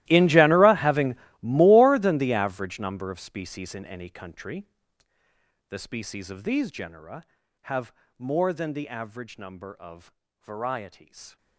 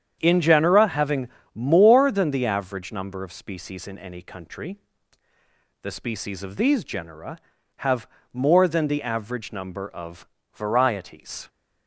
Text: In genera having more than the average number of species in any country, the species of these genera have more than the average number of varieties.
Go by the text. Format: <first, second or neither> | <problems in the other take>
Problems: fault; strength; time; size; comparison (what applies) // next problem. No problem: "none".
second | gets quieter; strong; throughout; 20 dB // starts louder than the rest; strong; until 1.0 s; 16 dB; strong in the second // pauses between "having" and "more"; slight; at 1.1 s; 0.24 s long; slight in the second // pauses between "have" and "more"; slight; at 7.9 s; 0.28 s long; slight in the second // pauses between "of" and "varieties"; slight; at 10.1 s; 0.30 s long; slight in the second